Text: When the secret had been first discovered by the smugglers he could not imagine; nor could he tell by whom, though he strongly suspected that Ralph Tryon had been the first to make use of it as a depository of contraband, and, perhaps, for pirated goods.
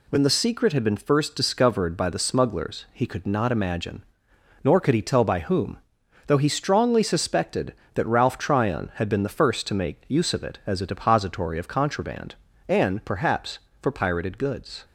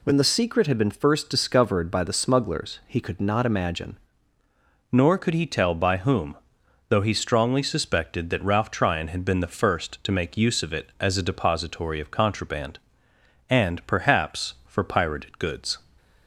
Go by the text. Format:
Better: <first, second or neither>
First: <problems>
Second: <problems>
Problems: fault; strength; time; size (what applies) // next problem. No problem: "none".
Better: first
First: none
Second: changes voice at "nor"; from 4.9 s on; 10.8 s long